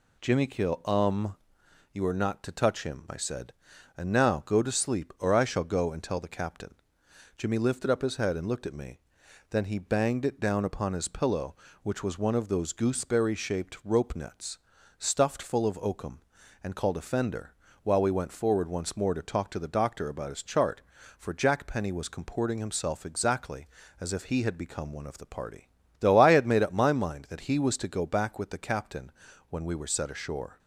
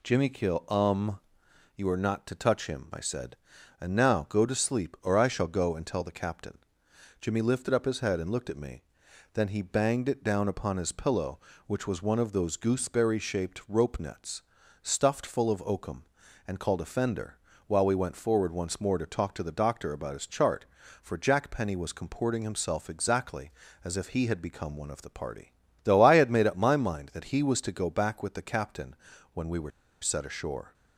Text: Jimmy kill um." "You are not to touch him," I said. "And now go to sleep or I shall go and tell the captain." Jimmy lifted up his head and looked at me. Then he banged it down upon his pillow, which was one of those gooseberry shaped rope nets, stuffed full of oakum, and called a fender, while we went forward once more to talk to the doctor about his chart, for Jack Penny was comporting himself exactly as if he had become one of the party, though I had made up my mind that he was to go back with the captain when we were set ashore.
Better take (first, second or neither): first